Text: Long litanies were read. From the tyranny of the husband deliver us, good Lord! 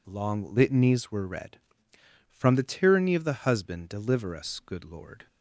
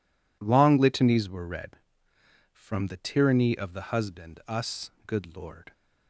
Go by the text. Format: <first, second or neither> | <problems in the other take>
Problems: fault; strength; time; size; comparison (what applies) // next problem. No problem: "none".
first | skips "deliver"; at 4.4 s